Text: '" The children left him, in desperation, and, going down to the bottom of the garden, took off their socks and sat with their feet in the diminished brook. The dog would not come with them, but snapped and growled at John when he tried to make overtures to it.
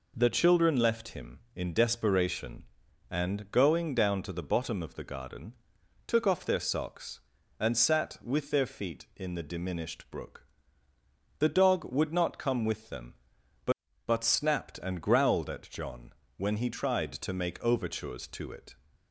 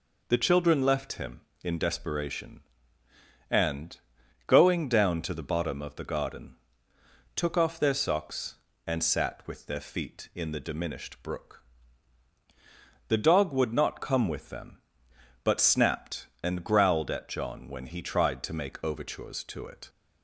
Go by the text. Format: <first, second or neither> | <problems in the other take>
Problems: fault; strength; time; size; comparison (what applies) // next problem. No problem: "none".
second | says "but" twice; at 14.0 s // pauses between "John" and "when"; slight; at 16.1 s; 0.24 s long